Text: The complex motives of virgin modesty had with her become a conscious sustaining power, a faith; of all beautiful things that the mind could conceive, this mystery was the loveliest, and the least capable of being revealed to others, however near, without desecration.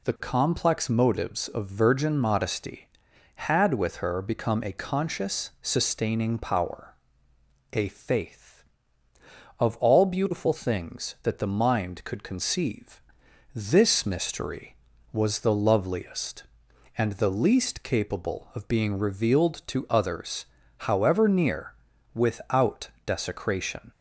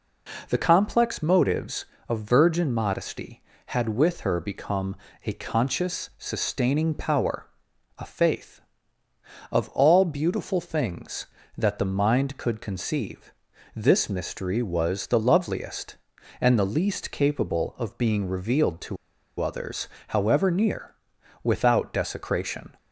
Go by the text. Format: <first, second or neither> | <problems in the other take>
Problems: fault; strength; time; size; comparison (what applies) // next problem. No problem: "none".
first | pauses between "become" and "a"; slight; at 4.9 s; 0.30 s long // pauses between "to" and "others"; at 18.9 s; 0.44 s long